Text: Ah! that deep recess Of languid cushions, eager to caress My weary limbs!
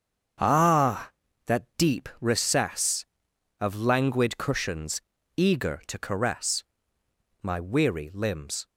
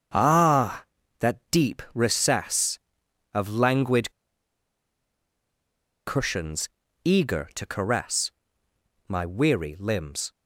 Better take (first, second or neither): first